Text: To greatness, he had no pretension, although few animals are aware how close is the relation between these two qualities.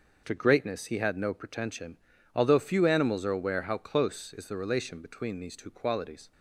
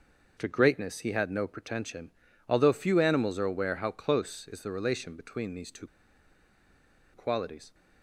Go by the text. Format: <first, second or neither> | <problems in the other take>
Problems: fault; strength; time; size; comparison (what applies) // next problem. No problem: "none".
first | pauses between "two" and "qualities"; strong; at 5.8 s; 1.2 s long